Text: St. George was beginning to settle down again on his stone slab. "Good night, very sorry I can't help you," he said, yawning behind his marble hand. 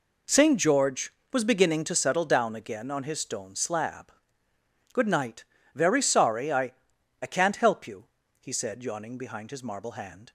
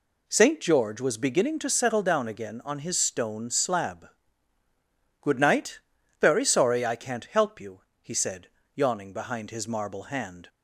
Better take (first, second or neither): second